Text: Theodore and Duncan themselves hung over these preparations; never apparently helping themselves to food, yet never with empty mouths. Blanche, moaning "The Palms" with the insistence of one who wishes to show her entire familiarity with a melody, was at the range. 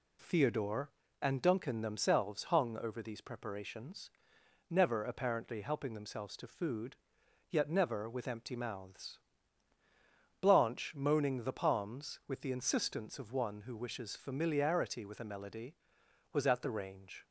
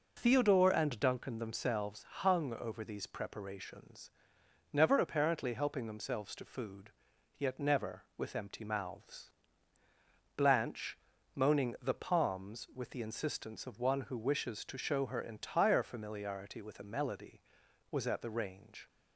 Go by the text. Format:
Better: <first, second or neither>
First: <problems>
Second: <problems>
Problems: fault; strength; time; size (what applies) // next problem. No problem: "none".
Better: second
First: skips "to show her entire"; at 14.1 s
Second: none